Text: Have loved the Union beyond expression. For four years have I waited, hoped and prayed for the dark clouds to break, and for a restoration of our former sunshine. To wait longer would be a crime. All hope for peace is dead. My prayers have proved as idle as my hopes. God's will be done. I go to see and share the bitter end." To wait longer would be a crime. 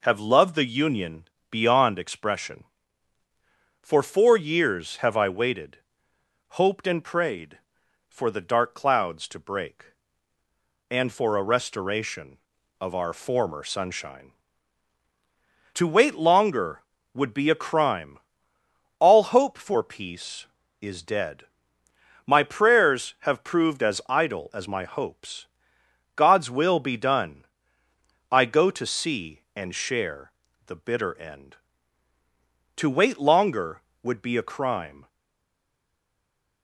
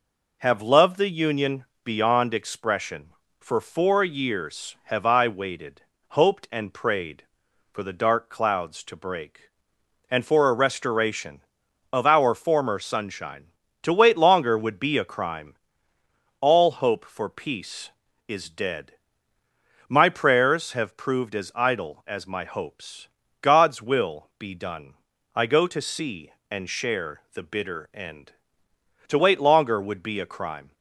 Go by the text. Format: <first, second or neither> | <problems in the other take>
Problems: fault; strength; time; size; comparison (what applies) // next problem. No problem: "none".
second | pauses between "Union" and "beyond"; slight; at 1.2 s; 0.26 s long; slight in the second // pauses between "share" and "the"; slight; at 30.2 s; 0.36 s long // stays silent after the last word; noticeable; from 35.0 s on; 1.6 s long